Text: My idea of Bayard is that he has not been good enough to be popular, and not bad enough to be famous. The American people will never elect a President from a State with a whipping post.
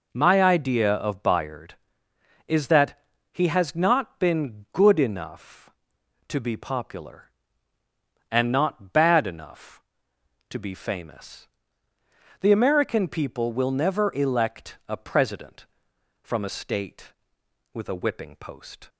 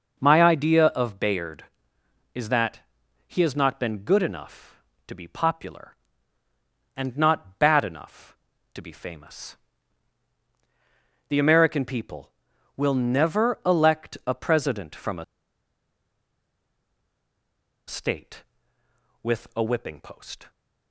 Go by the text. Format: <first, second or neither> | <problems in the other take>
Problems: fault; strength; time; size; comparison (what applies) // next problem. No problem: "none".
first | starts louder than the rest; noticeable; until 1.2 s; 6 dB // pauses between "that" and "he"; noticeable; at 2.7 s; 0.48 s long; slight in the first // pauses between "a" and "State"; strong; at 15.2 s; 2.6 s long